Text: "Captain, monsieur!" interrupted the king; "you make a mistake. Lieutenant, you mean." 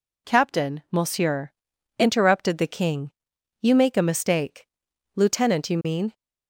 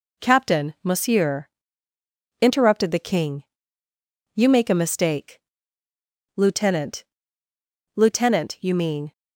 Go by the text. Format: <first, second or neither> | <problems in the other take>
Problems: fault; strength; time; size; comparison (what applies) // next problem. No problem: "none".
first | says "Lieutenant" twice; at 7.9 s